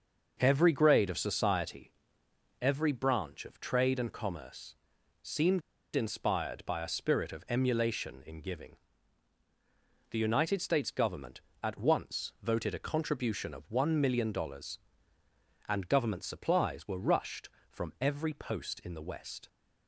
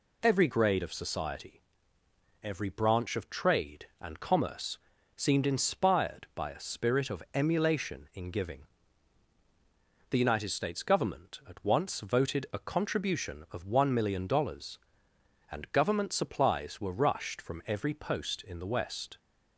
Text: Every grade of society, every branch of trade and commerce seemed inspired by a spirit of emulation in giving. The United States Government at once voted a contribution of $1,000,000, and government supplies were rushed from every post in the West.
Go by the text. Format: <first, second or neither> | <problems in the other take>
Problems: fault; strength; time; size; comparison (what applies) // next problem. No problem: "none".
second | starts louder than the rest; until 1.4 s; 6 dB // pauses between "commerce" and "seemed"; at 4.7 s; 0.44 s long; slight in the second // pauses between "seemed" and "inspired"; slight; at 5.6 s; 0.35 s long